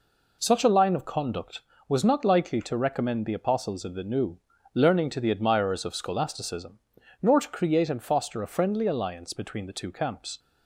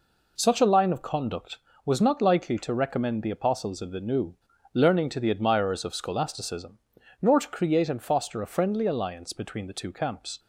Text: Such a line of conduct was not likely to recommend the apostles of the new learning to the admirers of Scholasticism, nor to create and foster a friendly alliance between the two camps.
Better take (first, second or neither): neither